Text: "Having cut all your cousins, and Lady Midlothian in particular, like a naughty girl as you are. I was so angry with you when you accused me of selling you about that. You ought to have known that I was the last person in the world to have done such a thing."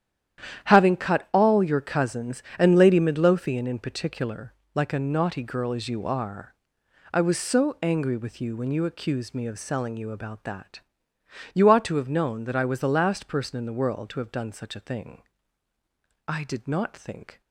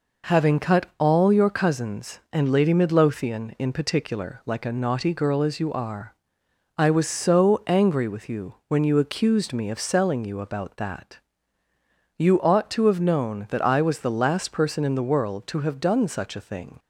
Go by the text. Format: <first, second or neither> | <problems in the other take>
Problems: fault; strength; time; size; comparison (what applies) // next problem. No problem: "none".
second | starts louder than the rest; strong; until 1.7 s; 10.5 dB // goes on to say "I did not think"; noticeable; from 16.2 s on; 1.1 s long